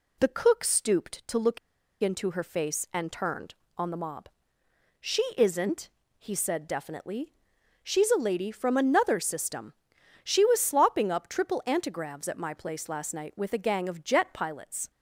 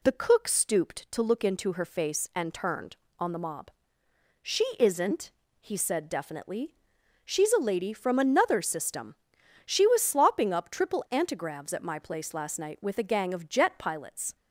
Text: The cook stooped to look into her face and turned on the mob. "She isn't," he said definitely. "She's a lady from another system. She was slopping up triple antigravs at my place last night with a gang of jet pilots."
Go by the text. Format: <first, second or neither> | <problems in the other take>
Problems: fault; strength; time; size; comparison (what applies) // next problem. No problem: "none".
second | pauses between "look" and "into"; at 1.5 s; 0.43 s long // pauses between "She" and "isn't"; slight; at 5.2 s; 0.16 s long; slight in the second